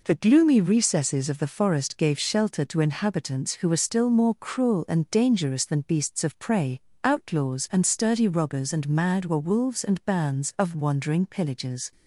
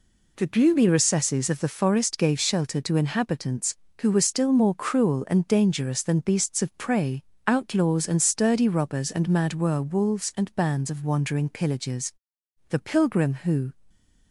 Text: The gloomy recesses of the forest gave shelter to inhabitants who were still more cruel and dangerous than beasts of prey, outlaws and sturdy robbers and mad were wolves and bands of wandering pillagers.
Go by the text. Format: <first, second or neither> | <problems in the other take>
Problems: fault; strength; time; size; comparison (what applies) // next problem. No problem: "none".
first | goes on to say "The pilgrim who"; noticeable; from 12.6 s on; 1.0 s long